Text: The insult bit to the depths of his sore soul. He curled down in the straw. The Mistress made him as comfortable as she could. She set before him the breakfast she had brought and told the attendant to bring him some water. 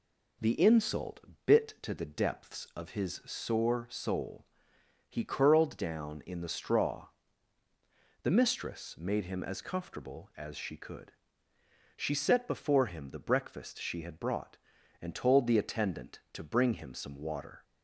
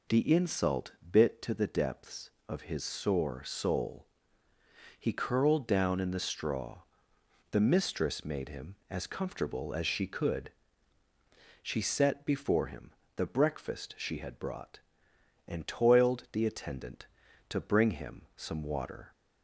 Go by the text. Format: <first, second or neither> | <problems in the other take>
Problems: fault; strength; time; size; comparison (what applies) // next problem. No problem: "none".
first | pauses between "insult" and "bit"; slight; at 0.9 s; 0.18 s long; slight in the first // pauses between "him" and "the"; slight; at 12.9 s; 0.24 s long // says "toiled" for "told"; at 15.6 s